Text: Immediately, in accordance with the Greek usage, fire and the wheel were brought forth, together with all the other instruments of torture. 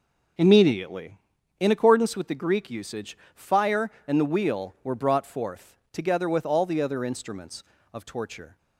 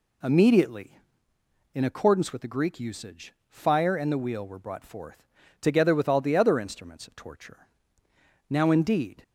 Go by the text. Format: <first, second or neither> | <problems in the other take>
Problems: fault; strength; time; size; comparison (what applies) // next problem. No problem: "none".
first | goes on to say "Now indeed"; noticeable; from 8.4 s on; 0.74 s long